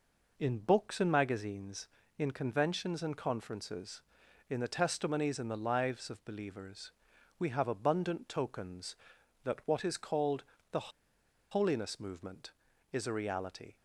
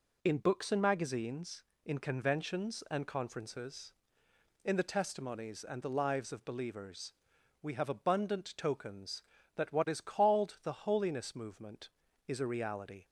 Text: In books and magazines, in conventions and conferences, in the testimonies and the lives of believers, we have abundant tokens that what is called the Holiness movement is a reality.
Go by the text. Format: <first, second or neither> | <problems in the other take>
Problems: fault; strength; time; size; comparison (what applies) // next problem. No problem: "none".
second | pauses between "called" and "the"; slight; at 10.4 s; 0.28 s long // pauses between "the" and "Holiness"; noticeable; at 10.9 s; 0.60 s long